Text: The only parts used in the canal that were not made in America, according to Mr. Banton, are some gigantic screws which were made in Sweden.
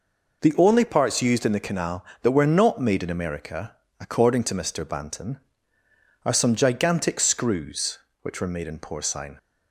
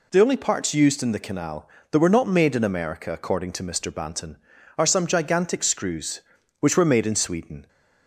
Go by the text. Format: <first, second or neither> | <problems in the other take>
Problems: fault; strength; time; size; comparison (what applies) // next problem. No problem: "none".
second | says "Porcine" for "Sweden"; at 8.7 s